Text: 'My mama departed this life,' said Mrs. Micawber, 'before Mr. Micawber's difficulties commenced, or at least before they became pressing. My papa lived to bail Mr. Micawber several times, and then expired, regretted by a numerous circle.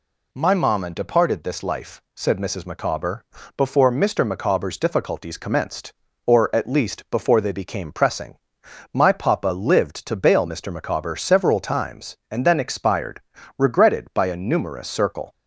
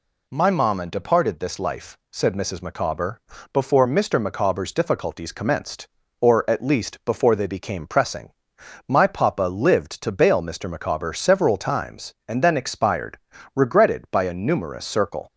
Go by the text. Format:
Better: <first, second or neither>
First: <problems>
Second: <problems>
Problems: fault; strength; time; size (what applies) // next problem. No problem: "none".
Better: neither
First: none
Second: none